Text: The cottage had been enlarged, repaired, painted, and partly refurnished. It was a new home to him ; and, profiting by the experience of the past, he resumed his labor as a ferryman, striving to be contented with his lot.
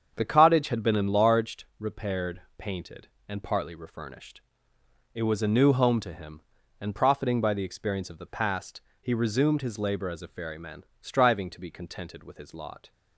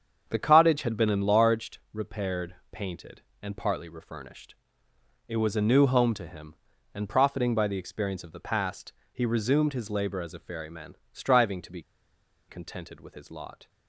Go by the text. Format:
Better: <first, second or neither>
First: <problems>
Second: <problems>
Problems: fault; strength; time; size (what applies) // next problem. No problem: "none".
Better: first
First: starts louder than the rest; strong; until 1.1 s; 7.5 dB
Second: starts louder than the rest; strong; until 1.2 s; 7.5 dB // pauses between "be" and "contented"; noticeable; at 11.8 s; 0.67 s long